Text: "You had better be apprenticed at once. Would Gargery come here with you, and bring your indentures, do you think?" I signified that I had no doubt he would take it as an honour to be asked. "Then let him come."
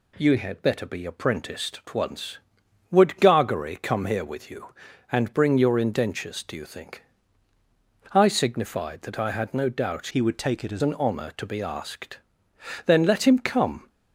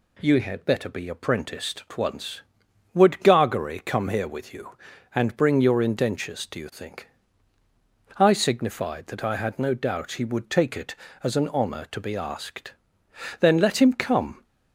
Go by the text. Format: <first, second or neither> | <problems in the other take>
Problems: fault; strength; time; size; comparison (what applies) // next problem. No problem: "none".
second | changes voice from "he" to "as"; from 10.0 to 10.8 s; 0.8 s long